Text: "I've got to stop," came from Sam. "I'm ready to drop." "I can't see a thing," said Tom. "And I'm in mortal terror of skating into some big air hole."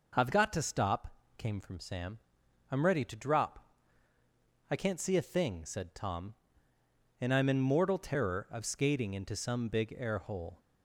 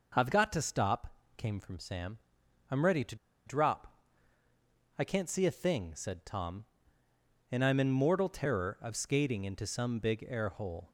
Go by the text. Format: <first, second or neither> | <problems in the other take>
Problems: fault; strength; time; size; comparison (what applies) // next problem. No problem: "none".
first | pauses between "to" and "drop"; slight; at 3.1 s; 0.31 s long